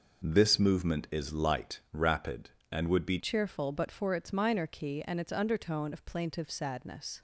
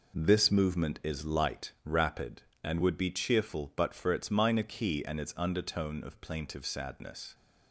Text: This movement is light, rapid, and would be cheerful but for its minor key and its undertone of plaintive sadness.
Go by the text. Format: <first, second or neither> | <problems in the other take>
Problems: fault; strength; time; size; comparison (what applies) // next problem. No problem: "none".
second | changes voice at "cheerful"; from 3.1 s on; 4.1 s long